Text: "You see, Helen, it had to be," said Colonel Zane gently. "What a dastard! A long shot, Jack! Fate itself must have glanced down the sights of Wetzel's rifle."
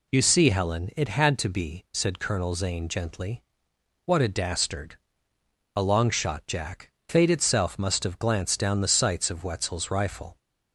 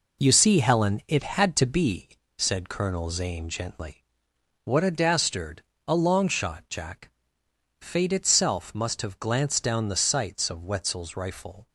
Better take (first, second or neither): first